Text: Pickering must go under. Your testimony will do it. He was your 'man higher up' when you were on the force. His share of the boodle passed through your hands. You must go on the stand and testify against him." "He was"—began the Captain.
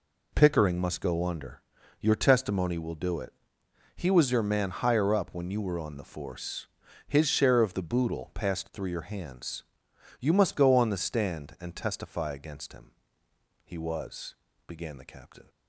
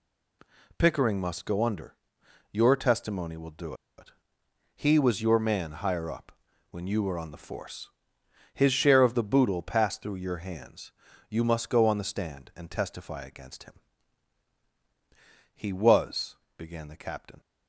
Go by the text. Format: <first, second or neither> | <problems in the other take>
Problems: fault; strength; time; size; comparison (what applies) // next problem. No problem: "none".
first | pauses between "do" and "it"; slight; at 3.7 s; 0.23 s long // pauses between "up" and "when"; at 6.3 s; 0.38 s long